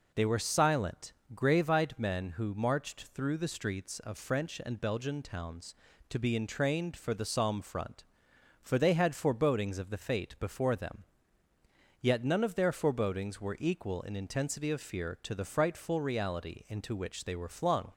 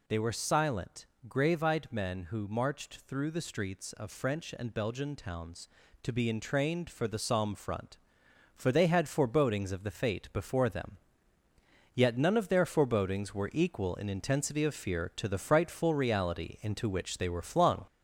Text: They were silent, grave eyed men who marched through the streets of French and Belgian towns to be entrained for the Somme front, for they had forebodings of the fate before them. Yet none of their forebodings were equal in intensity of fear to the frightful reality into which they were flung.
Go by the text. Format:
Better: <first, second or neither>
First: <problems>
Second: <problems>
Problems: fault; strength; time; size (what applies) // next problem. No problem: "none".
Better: first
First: none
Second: gets louder; noticeable; throughout; 4 dB